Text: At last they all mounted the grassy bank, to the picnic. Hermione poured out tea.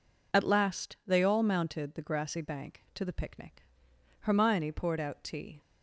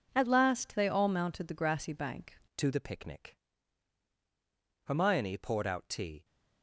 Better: first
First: none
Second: changes voice at "to"; from 2.5 s on; 3.7 s long

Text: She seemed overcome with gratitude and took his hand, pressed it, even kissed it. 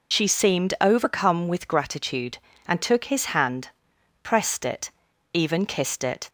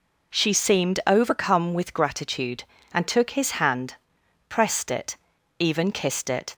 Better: second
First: loses the start of "She"; at 0.1 s; 40 ms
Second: none

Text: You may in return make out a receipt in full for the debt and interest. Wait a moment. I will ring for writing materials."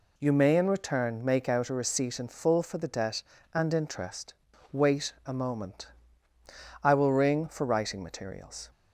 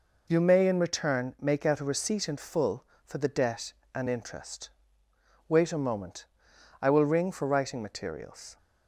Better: neither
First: none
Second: none

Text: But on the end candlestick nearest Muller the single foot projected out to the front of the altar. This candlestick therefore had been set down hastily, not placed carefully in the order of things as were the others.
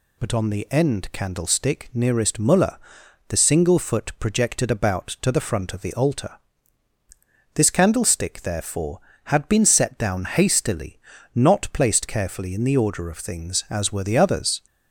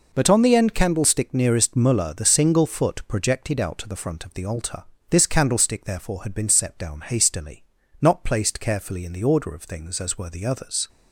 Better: second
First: pauses between "Muller" and "the"; noticeable; at 2.7 s; 0.52 s long // says "about" for "out"; at 4.7 s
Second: none

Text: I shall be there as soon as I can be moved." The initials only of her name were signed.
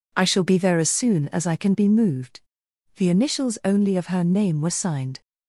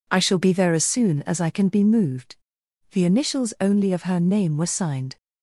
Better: neither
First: none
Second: none

